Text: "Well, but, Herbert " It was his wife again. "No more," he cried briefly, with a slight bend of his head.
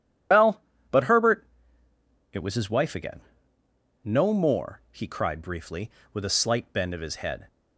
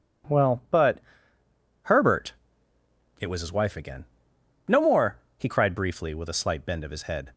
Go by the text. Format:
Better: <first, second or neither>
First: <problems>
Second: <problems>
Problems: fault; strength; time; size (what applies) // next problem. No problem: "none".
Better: second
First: loses the start of "Well"; at 0.3 s; 75 ms // starts louder than the rest; strong; until 2.0 s; 10 dB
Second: none